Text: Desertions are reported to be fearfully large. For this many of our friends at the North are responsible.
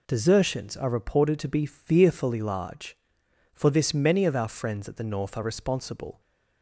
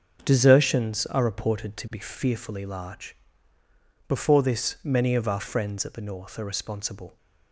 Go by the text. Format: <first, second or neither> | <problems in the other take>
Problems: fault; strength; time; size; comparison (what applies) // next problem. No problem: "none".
first | starts louder than the rest; until 1.2 s; 6.5 dB // says "Before" for "For"; at 4.0 s